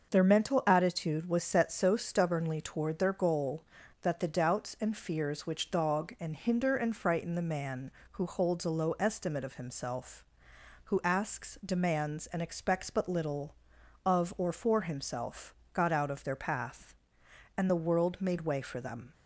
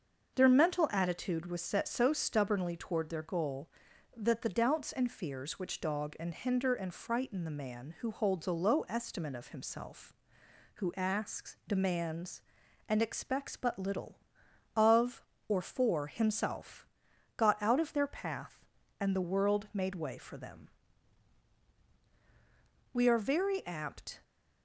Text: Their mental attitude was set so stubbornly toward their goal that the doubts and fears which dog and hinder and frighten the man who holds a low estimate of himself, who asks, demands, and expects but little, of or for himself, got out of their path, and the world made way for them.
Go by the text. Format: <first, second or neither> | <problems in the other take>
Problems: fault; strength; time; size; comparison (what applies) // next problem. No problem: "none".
first | starts louder than the rest; until 1.3 s; 6.5 dB; also in the first // goes on to say "We are very apt"; noticeable; from 22.9 s on; 1.2 s long